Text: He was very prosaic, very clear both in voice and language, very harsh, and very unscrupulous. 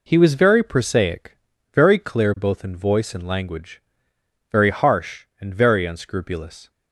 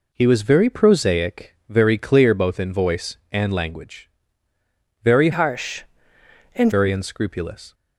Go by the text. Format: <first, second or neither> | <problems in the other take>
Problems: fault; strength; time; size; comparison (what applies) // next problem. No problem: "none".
first | changes voice from "harsh" to "and"; from 5.3 to 6.7 s; 1.4 s long